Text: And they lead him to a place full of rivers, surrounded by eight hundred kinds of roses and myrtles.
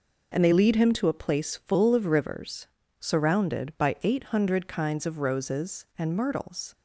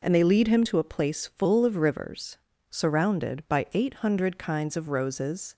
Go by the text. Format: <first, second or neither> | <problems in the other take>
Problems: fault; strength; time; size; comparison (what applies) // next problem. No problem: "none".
first | stops before "and myrtles"; at 5.5 s